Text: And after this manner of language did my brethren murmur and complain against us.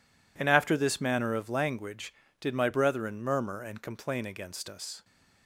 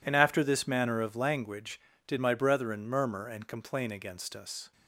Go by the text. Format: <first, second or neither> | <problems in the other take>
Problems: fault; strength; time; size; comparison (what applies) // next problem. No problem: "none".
neither | none